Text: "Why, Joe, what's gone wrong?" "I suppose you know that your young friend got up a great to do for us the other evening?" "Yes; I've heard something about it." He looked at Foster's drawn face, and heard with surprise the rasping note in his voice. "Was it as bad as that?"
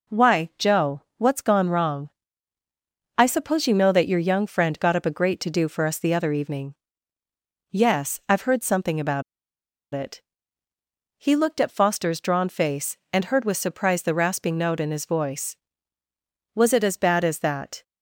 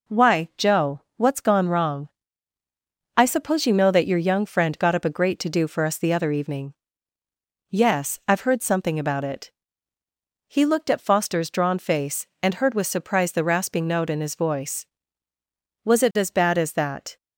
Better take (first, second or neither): second